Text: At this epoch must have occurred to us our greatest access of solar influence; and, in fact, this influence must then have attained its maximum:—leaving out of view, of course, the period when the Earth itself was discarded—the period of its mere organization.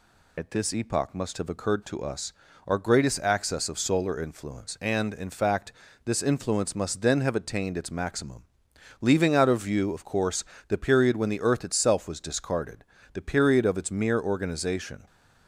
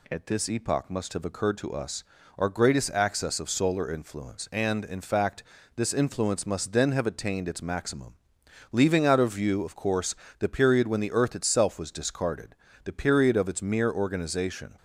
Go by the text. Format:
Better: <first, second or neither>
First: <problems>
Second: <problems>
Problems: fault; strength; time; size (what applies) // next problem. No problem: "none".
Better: second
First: loses the start of "At"; at 0.3 s; 75 ms // pauses between "us" and "our"; slight; at 2.3 s; 0.34 s long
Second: pauses between "us" and "our"; slight; at 2.0 s; 0.34 s long